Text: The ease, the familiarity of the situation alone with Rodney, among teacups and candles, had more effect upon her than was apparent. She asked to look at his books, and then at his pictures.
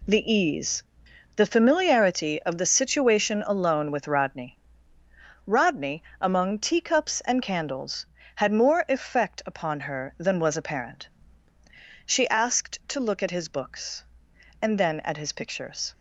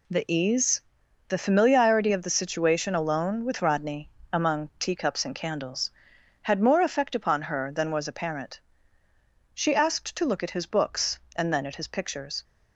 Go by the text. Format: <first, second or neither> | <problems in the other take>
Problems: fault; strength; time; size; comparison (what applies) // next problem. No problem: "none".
second | says "Rodney" twice; at 5.4 s